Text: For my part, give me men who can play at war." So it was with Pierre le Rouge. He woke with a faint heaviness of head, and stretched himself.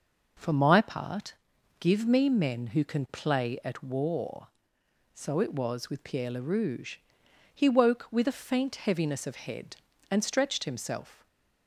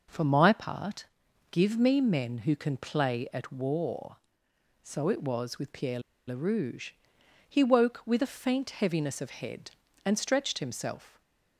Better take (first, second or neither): first